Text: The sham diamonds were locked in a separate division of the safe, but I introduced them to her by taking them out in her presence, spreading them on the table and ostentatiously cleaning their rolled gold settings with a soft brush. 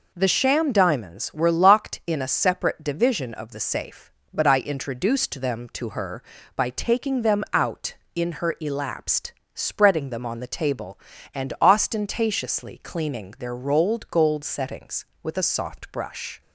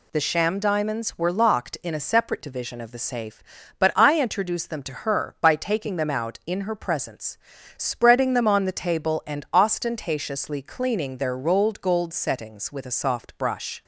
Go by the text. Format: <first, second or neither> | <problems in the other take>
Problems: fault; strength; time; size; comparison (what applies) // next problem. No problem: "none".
second | says "elapsed" for "presence"; at 8.5 s